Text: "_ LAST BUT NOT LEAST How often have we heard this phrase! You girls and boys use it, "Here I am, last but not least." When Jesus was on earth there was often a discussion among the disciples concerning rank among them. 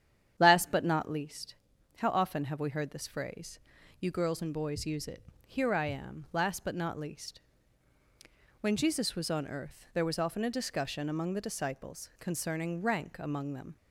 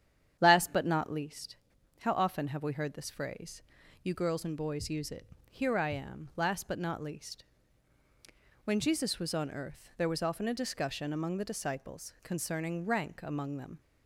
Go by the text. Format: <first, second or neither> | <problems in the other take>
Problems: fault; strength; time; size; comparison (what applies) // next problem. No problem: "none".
neither | starts louder than the rest; strong; the same in both // pauses between "LEAST" and "How"; the same in both